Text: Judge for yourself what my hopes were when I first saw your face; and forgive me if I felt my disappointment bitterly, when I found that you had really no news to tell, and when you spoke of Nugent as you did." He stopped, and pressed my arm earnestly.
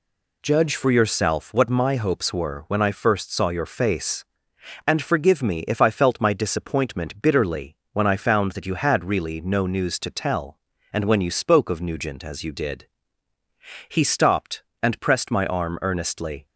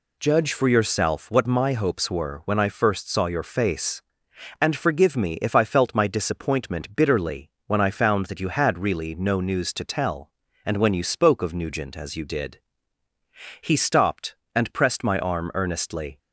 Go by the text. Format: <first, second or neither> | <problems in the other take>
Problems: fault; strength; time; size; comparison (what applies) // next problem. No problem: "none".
neither | none